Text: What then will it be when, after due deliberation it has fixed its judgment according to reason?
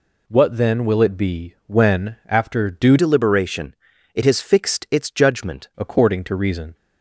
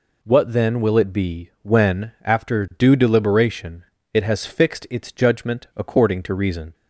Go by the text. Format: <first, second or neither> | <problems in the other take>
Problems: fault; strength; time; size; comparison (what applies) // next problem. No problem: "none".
second | changes voice from "deliberation" to "judgment"; from 2.9 to 5.6 s; 2.7 s long // pauses between "deliberation" and "it"; at 3.7 s; 0.40 s long; slight in the second